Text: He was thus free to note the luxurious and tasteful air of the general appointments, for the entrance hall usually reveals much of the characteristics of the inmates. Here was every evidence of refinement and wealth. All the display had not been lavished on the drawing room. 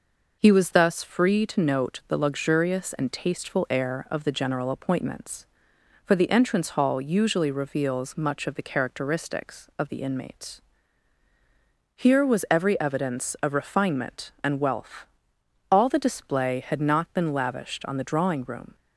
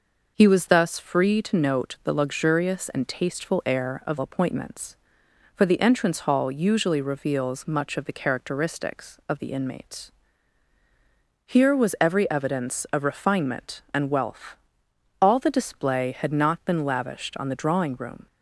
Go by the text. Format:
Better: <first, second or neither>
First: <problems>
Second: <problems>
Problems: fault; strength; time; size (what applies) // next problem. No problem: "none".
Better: first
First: none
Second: skips "the general"; at 4.1 s